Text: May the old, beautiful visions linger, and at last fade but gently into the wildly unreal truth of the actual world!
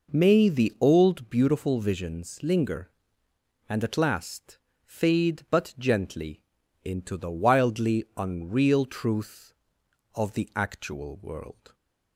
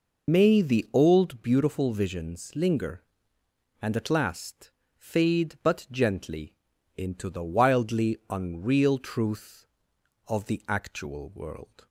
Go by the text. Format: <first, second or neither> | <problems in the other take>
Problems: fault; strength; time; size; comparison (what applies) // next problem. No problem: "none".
first | loses the start of "May"; at 0.2 s; 70 ms // pauses between "last" and "fade"; slight; at 4.7 s; 0.26 s long; slight in the first // pauses between "gently" and "into"; at 6.5 s; 0.42 s long; also in the first